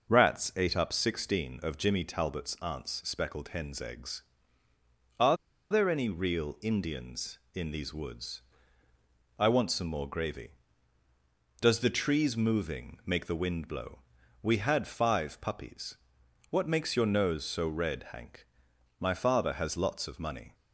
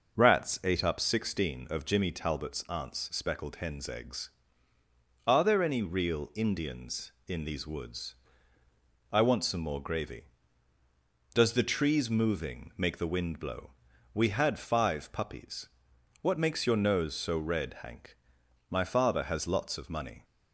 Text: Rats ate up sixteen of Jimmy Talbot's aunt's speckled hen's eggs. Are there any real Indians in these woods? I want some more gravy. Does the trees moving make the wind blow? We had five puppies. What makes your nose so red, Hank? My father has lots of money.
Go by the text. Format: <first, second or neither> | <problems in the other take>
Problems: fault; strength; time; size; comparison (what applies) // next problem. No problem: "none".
second | pauses between "Are" and "there"; slight; at 5.3 s; 0.34 s long